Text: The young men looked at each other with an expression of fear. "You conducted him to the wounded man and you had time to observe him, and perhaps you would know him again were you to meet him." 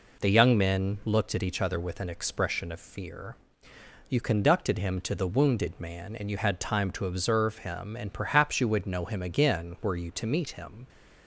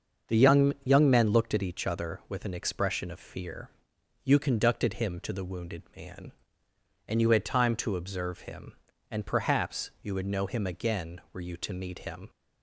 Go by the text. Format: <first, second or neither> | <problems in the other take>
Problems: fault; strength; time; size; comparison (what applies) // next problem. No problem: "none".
first | starts louder than the rest; until 1.4 s; 6.5 dB // says "young" twice; at 0.8 s